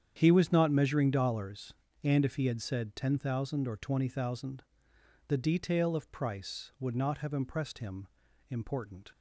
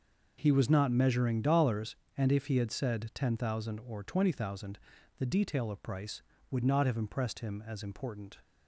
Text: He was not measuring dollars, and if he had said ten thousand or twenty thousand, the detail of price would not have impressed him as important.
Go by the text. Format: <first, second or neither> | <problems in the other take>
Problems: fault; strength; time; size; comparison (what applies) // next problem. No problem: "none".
second | starts louder than the rest; strong; until 1.2 s; 9 dB // skips "as"; at 8.2 s